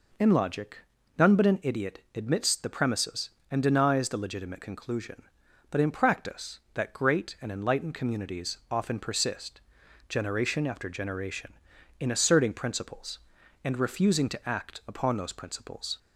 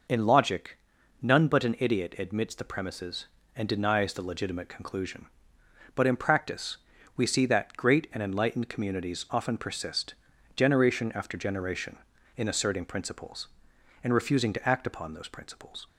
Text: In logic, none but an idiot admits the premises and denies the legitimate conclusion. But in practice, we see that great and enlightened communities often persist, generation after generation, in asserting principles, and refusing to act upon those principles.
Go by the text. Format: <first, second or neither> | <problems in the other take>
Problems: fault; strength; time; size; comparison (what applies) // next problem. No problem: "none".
second | skips "we see"; at 6.6 s